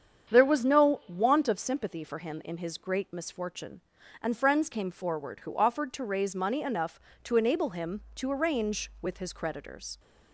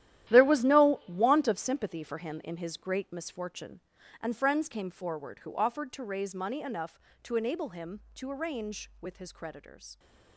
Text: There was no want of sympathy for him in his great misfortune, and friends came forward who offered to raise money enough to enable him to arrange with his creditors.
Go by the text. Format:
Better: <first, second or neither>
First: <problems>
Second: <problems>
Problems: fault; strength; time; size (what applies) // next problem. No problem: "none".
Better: first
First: starts louder than the rest; strong; until 1.3 s; 8 dB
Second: gets quieter; strong; throughout; 12.5 dB // starts louder than the rest; strong; until 1.3 s; 12.5 dB